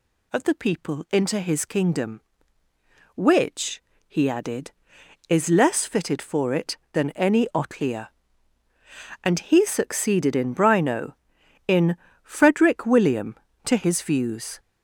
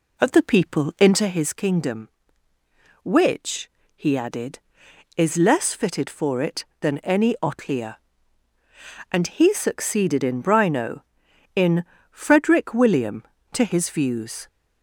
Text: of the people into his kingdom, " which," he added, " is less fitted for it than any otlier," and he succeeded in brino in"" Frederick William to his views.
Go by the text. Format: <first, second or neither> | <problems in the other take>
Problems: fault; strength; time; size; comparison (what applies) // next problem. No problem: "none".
first | starts louder than the rest; until 1.4 s; 3.5 dB // pauses between "in" and "Frederick"; slight; at 11.8 s; 0.28 s long; slight in the first